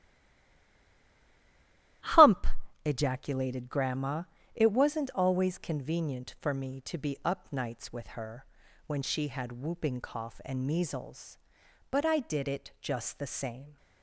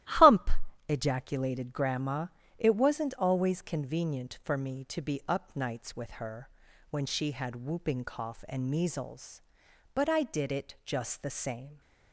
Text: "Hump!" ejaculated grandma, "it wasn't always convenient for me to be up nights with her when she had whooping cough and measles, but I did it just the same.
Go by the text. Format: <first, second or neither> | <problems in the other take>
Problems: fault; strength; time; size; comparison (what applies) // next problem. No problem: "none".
second | stays silent before the first word; noticeable; until 2.0 s; 2.0 s long // starts louder than the rest; strong; until 3.4 s; 14.5 dB; strong in the second // pauses between "her" and "when"; at 8.4 s; 0.42 s long; also in the second